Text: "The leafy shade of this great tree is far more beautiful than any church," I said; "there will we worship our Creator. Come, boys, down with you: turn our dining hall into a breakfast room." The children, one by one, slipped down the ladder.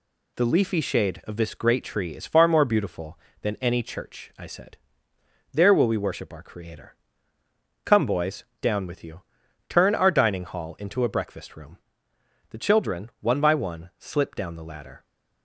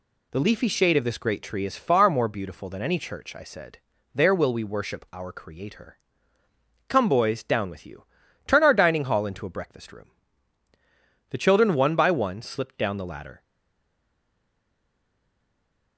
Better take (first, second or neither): first